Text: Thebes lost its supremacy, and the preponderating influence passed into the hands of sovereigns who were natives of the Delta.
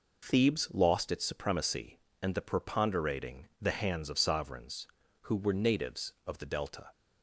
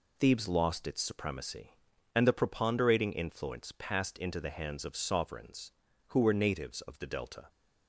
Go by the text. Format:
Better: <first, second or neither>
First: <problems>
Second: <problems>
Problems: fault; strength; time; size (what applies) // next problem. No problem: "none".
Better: second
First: skips "influence passed into"; at 3.5 s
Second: none